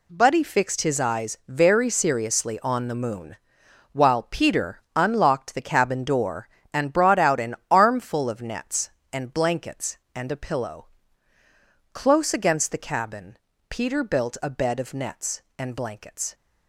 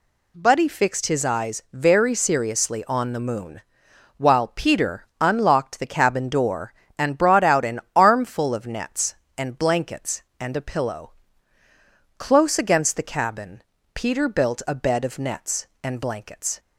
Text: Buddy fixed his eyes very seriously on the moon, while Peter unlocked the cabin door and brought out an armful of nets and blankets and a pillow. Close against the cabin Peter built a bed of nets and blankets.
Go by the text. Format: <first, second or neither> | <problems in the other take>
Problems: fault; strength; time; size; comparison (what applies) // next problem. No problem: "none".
second | gets quieter; strong; throughout; 10.5 dB // pauses between "Peter" and "unlocked"; slight; at 4.8 s; 0.16 s long; slight in the second // pauses between "an" and "armful"; slight; at 7.5 s; 0.16 s long; slight in the second // pauses between "cabin" and "Peter"; slight; at 13.3 s; 0.32 s long; slight in the second